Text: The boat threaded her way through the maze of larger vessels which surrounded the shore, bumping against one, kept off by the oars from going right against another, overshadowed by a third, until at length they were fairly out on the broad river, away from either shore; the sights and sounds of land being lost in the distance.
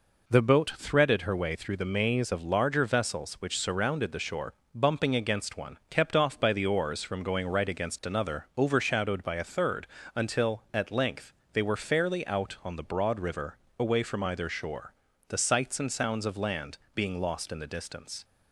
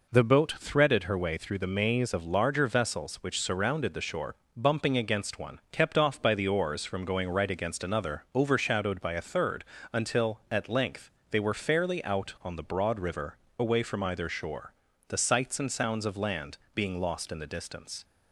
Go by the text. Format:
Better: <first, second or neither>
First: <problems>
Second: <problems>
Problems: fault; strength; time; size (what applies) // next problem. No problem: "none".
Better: neither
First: pauses between "length" and "they"; slight; at 11.3 s; 0.20 s long // pauses between "land" and "being"; slight; at 16.7 s; 0.16 s long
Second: pauses between "length" and "they"; slight; at 11.0 s; 0.20 s long // pauses between "land" and "being"; slight; at 16.5 s; 0.16 s long